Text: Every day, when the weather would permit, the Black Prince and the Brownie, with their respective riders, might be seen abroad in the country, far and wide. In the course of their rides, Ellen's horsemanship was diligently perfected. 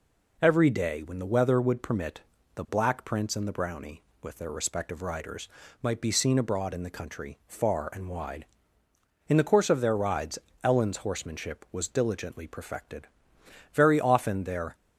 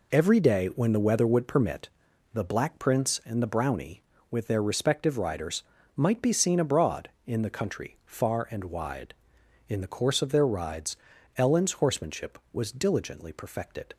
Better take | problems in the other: second | goes on to say "Very often their"; noticeable; from 13.7 s on; 1.0 s long

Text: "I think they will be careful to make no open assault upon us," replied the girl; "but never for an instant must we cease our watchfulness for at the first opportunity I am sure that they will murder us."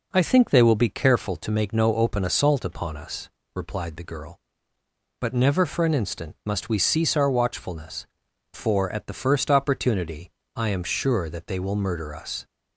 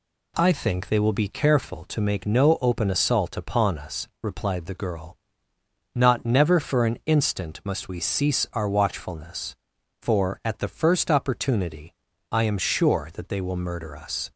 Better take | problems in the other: first | says "not" for "but"; at 5.9 s // pauses between "opportunity" and "I"; at 11.9 s; 0.38 s long; slight in the first

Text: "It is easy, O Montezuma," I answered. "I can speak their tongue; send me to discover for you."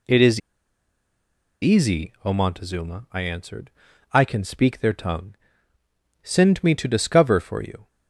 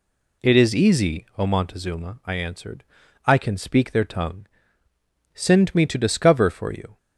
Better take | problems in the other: second | pauses between "is" and "easy"; at 0.3 s; 1.2 s long

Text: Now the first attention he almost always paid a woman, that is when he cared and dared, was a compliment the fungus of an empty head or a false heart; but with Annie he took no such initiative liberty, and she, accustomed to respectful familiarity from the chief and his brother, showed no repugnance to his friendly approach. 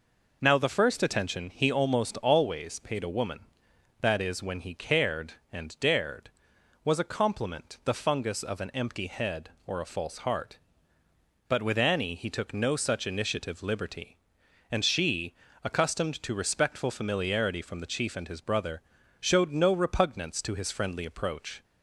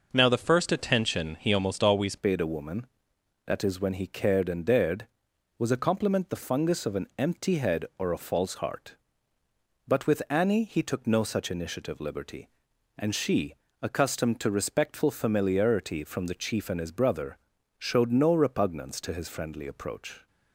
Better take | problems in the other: first | changes voice at "paid"; from 2.1 s on; 18.1 s long

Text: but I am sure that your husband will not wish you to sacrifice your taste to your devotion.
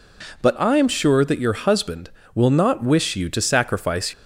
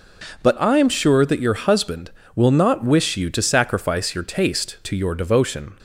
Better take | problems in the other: second | stops before "your taste to your devotion"; at 4.1 s

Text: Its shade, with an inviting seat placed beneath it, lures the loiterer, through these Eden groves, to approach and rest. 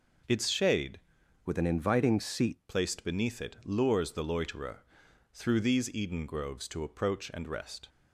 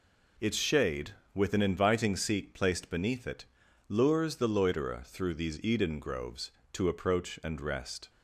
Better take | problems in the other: second | changes voice from "with" to "seat"; from 1.4 to 2.6 s; 1.2 s long

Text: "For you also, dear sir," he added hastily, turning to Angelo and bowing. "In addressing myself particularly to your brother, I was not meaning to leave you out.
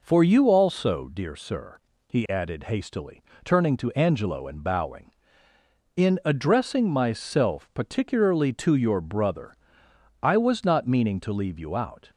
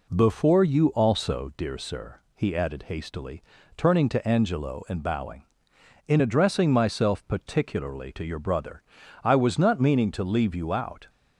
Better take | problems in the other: first | says "Before" for "For"; at 0.1 s

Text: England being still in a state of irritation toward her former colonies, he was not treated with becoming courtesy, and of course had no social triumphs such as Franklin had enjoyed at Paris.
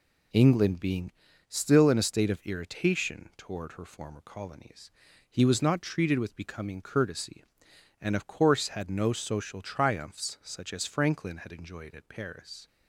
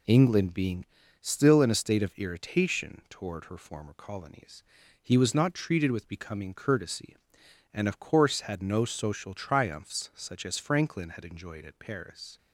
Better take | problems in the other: neither | pauses between "being" and "still"; the same in both

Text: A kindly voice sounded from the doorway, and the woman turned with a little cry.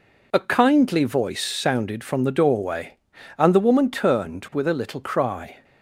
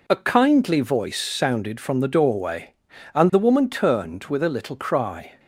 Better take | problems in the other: neither | none

